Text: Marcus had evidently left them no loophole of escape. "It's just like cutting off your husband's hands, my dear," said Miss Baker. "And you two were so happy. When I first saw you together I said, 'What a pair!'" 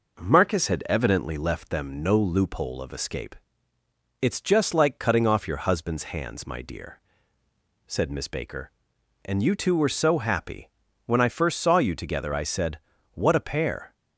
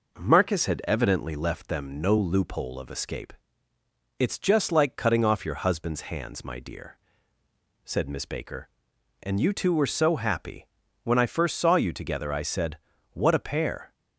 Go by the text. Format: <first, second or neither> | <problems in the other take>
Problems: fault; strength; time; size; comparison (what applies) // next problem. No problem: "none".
neither | none